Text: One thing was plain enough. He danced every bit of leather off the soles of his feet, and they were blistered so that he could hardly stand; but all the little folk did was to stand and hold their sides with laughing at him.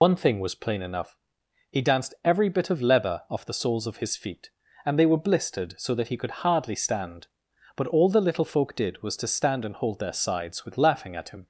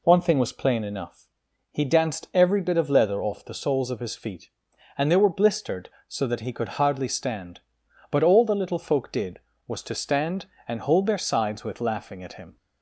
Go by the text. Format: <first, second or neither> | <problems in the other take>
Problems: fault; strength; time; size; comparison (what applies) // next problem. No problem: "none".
second | loses the start of "One"; at 0.0 s; 95 ms